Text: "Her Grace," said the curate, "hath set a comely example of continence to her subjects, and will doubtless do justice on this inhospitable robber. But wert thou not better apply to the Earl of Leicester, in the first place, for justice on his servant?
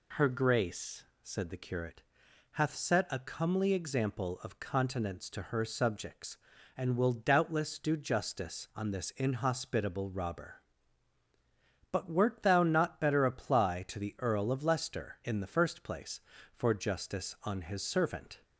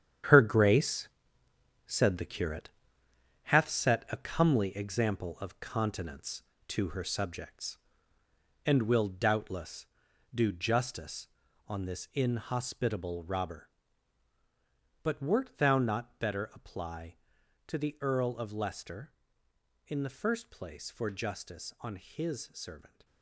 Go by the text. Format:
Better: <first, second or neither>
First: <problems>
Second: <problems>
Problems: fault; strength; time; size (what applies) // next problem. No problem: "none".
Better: first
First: none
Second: gets quieter; strong; throughout; 10.5 dB